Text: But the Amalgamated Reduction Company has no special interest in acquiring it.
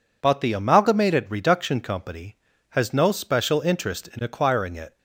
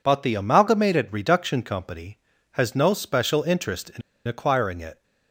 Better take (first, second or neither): first